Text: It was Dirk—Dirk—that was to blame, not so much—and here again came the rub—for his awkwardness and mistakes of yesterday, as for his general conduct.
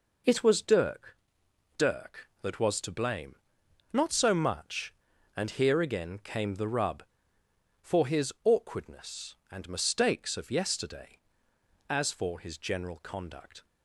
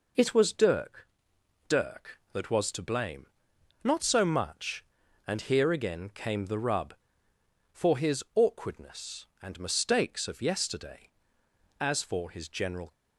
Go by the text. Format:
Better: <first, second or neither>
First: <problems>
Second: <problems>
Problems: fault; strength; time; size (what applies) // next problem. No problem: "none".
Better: first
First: none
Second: stops before "conduct"; at 12.9 s